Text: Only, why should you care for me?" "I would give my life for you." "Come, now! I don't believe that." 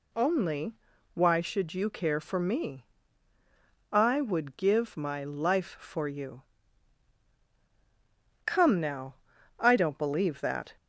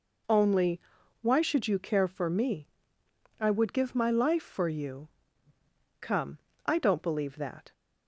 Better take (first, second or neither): first